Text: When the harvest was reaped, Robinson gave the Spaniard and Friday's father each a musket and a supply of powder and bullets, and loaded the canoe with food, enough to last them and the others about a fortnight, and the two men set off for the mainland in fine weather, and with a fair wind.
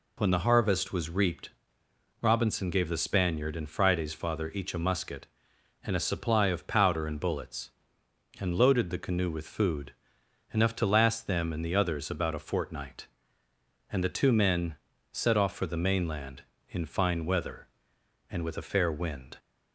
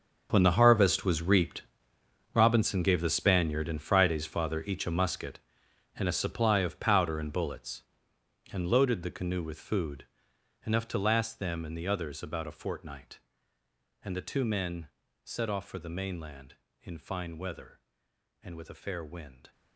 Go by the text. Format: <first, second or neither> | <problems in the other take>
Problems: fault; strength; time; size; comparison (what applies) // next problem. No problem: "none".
first | gets quieter; strong; throughout; 15.5 dB // pauses between "men" and "set"; at 14.8 s; 0.38 s long; also in the first